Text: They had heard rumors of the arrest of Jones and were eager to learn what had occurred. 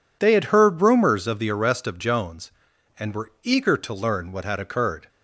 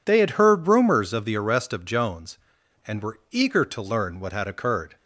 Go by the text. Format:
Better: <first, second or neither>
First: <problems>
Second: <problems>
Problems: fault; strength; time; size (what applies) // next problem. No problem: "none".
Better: neither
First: none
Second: none